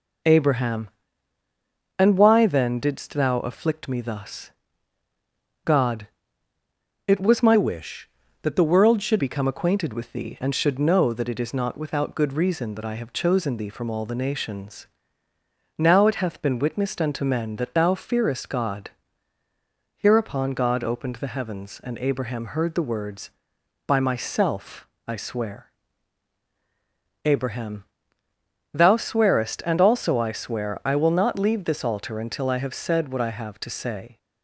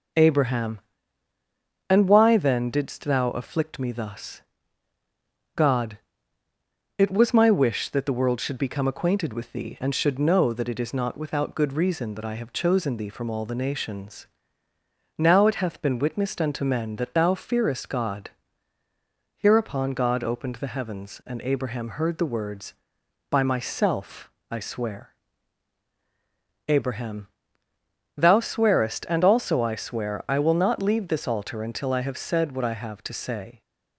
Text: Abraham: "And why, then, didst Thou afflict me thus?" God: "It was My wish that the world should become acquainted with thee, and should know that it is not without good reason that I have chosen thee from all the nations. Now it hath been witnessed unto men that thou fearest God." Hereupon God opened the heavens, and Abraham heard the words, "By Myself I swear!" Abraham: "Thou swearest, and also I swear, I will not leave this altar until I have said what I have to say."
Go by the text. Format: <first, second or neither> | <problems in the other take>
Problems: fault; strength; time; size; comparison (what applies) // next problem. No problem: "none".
second | changes voice from "wish" to "should"; from 7.5 to 9.1 s; 1.6 s long // pauses between "Myself" and "I"; slight; at 24.8 s; 0.20 s long; slight in the second